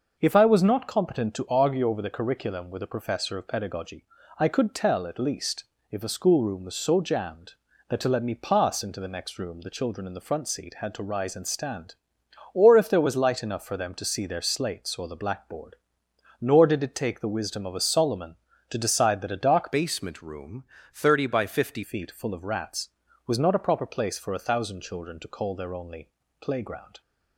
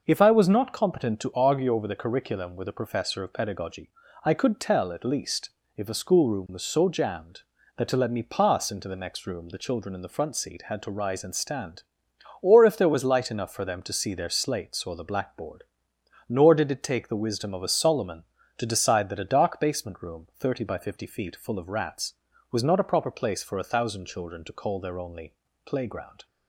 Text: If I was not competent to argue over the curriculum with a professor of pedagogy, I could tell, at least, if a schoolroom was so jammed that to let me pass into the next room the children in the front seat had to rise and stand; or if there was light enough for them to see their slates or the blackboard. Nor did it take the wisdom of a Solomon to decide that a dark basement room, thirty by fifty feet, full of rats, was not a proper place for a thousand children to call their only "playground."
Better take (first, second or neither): second